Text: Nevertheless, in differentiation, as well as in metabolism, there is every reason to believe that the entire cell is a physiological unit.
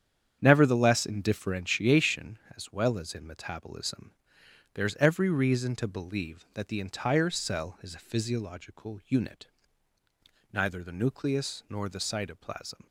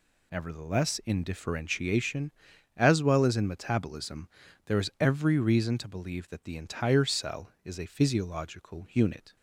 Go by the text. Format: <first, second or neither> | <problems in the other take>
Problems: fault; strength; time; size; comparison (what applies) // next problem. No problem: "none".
second | starts louder than the rest; strong; until 1.4 s; 8.5 dB // goes on to say "Neither the nucleus nor the cytoplasm"; strong; from 10.5 s on; 2.3 s long